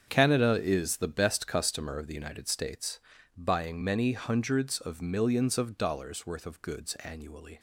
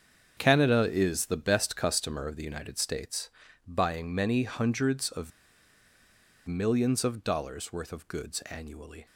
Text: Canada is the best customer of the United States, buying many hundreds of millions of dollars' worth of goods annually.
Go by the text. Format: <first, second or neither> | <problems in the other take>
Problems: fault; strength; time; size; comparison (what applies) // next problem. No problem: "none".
first | starts louder than the rest; strong; until 1.3 s; 7 dB; strong in the first // pauses between "of" and "millions"; at 5.3 s; 1.1 s long